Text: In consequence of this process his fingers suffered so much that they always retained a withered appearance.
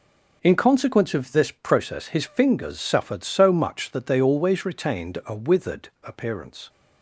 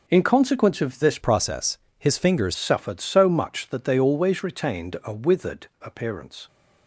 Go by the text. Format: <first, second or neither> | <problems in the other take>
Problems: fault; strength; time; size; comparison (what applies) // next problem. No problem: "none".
first | changes voice from "process" to "fingers"; from 1.2 to 2.5 s; 1.3 s long // pauses between "process" and "his"; slight; at 1.7 s; 0.22 s long